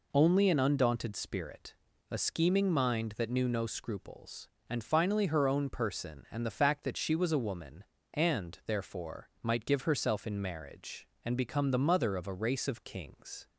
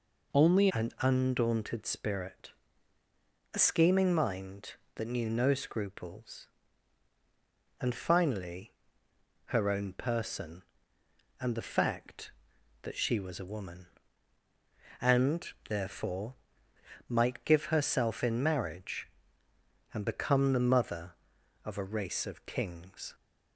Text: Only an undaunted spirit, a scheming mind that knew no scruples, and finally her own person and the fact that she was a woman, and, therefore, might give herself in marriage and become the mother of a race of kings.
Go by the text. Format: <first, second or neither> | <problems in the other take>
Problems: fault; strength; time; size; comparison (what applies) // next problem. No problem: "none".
first | changes voice at "an"; from 0.7 s on; 22.4 s long // pauses between "finally" and "her"; noticeable; at 8.7 s; 0.74 s long